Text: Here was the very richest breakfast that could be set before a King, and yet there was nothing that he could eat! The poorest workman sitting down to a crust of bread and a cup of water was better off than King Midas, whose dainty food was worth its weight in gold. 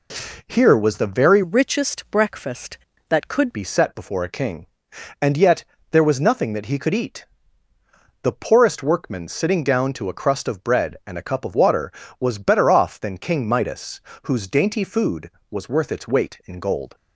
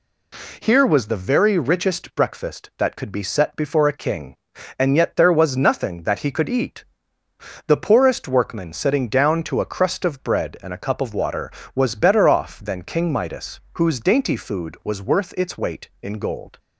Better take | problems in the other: second | changes voice from "richest" to "could"; from 1.4 to 3.5 s; 2.1 s long // pauses between "yet" and "there"; slight; at 5.6 s; 0.28 s long

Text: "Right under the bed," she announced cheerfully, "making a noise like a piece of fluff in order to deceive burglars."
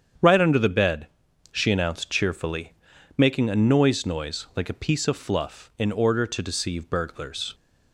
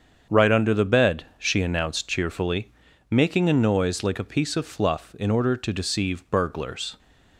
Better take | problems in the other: second | starts louder than the rest; strong; until 1.6 s; 8 dB; strong in the second // says "noise" twice; at 4.0 s

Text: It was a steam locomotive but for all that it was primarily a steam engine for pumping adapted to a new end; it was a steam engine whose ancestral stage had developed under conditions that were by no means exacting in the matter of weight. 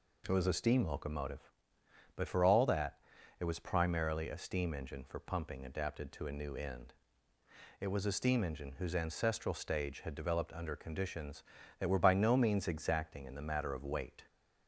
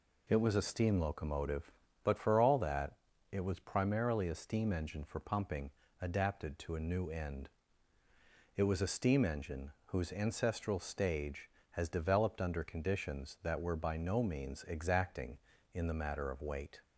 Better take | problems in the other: first | pauses between "that" and "it"; slight; at 2.9 s; 0.36 s long; also in the first // pauses between "pumping" and "adapted"; slight; at 5.7 s; 0.32 s long // says "has" for "had"; at 11.7 s

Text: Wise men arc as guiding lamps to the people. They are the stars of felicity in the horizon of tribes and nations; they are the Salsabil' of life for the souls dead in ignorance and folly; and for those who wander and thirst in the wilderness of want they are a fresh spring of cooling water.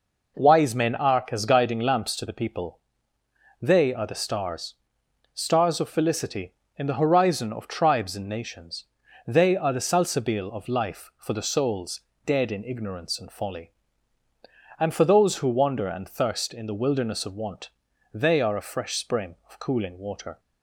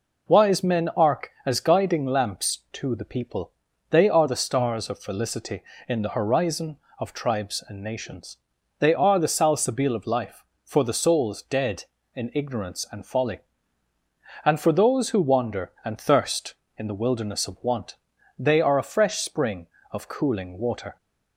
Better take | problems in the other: second | says "stars" twice; at 5.3 s // pauses between "souls" and "dead"; slight; at 11.9 s; 0.26 s long // pauses between "want" and "they"; at 17.6 s; 0.44 s long; also in the second

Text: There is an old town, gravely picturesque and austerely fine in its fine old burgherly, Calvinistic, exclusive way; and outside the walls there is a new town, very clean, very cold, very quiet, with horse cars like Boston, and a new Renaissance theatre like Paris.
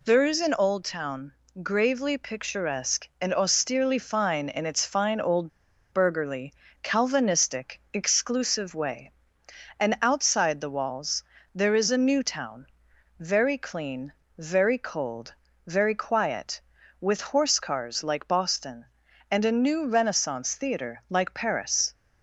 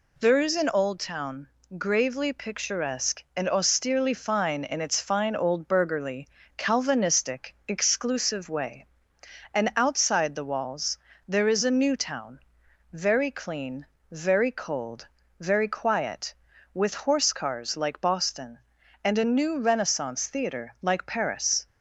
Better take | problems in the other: second | pauses between "old" and "burgherly"; at 5.5 s; 0.42 s long // pauses between "walls" and "there"; slight; at 11.2 s; 0.32 s long; slight in the second

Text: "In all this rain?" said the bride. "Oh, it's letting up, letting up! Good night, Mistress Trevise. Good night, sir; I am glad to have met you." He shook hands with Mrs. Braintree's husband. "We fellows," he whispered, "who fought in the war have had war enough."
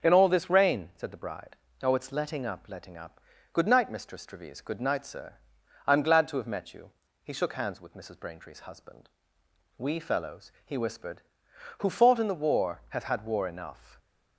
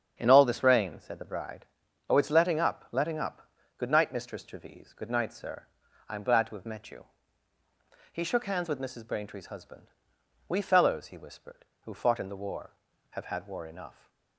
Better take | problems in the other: neither | starts louder than the rest; the same in both

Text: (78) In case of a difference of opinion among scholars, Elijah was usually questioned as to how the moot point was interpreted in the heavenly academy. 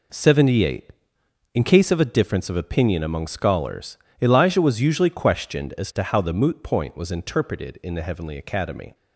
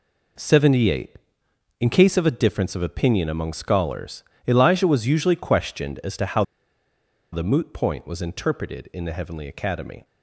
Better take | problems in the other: first | pauses between "how" and "the"; noticeable; at 6.4 s; 0.89 s long

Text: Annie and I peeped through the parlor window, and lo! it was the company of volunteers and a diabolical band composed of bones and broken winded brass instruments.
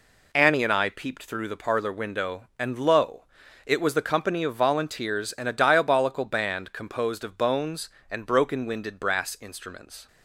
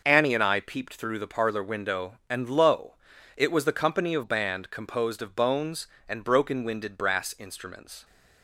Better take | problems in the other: first | skips "volunteers and a diabolical"; at 4.2 s

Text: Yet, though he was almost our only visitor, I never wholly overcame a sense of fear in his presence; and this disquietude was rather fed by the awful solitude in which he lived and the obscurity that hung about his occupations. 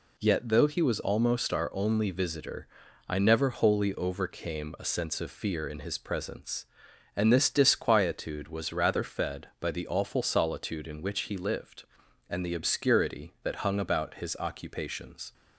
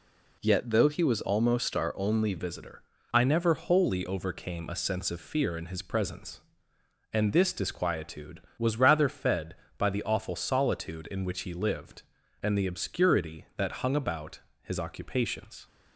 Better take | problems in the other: first | changes voice at "visitor"; from 2.3 s on; 13.3 s long // pauses between "about" and "his"; slight; at 14.4 s; 0.20 s long

